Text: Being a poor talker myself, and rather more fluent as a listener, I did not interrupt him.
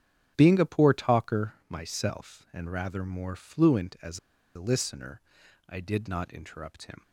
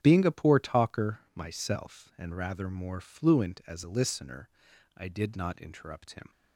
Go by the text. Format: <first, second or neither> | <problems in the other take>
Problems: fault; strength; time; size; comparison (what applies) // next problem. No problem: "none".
second | starts louder than the rest; strong; until 1.3 s; 8.5 dB; strong in the second // pauses between "talker" and "myself"; slight; at 1.5 s; 0.16 s long; slight in the second // pauses between "as" and "a"; at 4.1 s; 0.36 s long